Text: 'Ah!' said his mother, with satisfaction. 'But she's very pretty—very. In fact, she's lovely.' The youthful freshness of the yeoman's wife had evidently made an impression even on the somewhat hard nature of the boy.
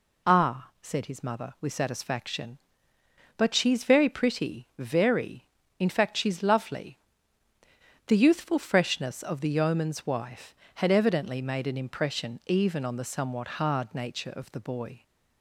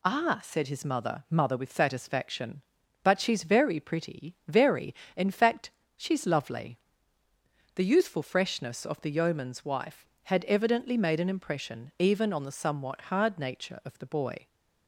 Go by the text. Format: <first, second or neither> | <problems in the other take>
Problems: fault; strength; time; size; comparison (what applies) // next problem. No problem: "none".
first | says "mother" twice; at 1.2 s